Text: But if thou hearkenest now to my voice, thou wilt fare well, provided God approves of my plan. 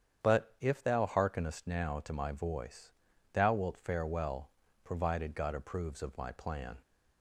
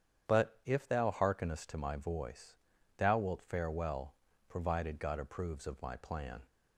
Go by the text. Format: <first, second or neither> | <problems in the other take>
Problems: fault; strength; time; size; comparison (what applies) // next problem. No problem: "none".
first | starts louder than the rest; strong; until 1.3 s; 8.5 dB; strong in the first // skips "now"; at 1.6 s